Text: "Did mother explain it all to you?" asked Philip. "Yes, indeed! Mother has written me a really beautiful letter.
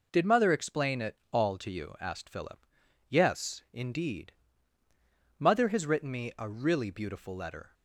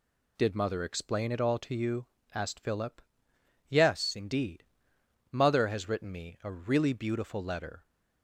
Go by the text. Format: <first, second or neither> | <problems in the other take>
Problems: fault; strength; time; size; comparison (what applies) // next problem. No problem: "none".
neither | none